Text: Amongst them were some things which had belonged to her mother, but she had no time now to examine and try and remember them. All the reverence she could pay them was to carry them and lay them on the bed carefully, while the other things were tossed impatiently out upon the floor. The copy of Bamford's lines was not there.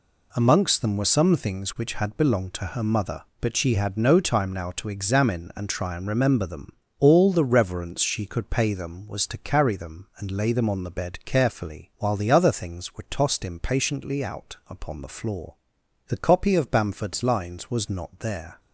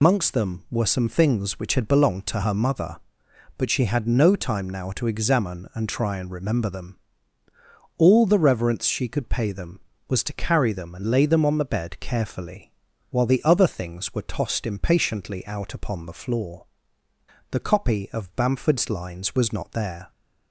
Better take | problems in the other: first | loses the start of "Amongst"; at 0.0 s; 90 ms

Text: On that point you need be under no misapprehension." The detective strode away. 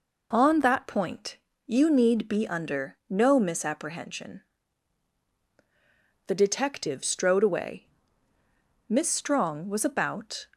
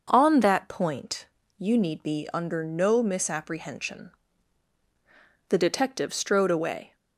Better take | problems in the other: second | pauses between "point" and "you"; slight; at 1.3 s; 0.30 s long; slight in the second // goes on to say "Miss Strong was about"; from 8.8 s on; 1.5 s long

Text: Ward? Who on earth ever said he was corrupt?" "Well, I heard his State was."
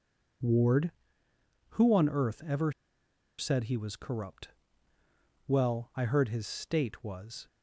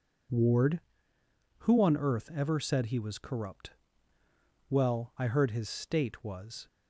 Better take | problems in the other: second | pauses between "ever" and "said"; noticeable; at 2.7 s; 0.66 s long

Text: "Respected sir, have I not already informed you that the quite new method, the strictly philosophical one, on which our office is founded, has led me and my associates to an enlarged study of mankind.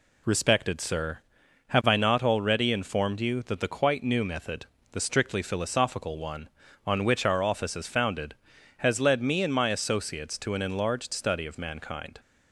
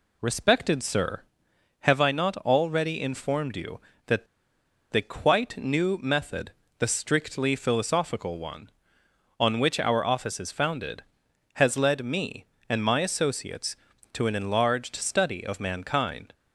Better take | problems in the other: first | pauses between "that" and "the"; noticeable; at 4.2 s; 0.65 s long

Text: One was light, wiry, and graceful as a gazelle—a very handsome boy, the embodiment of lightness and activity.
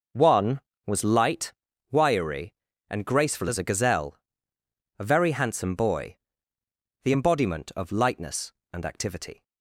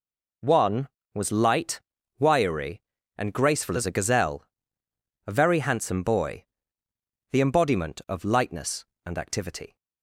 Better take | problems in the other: second | starts louder than the rest; noticeable; until 1.3 s; 5.5 dB

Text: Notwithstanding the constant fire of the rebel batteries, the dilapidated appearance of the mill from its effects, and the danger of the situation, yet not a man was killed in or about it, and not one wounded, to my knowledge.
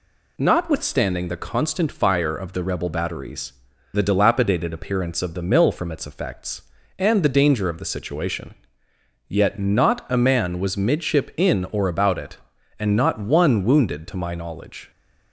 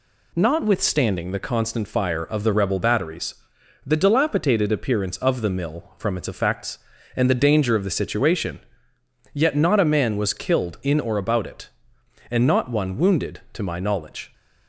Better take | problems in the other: second | says "midship" for "killed"; at 10.7 s

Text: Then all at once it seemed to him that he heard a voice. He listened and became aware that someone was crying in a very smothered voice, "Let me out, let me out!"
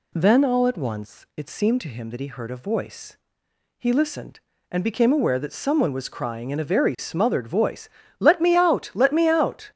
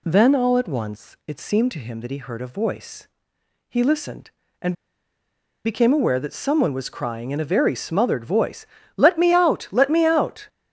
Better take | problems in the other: first | pauses between "and" and "became"; noticeable; at 4.7 s; 0.90 s long

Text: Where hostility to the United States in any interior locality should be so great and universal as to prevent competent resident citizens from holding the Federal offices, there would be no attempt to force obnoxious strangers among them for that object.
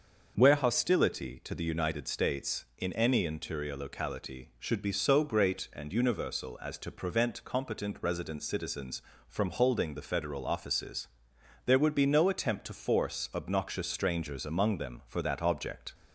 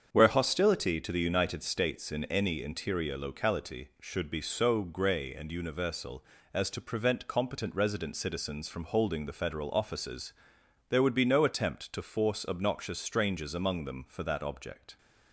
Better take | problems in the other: first | starts louder than the rest; strong; until 1.1 s; 7.5 dB; also in the first // says "grey" for "great"; at 4.8 s

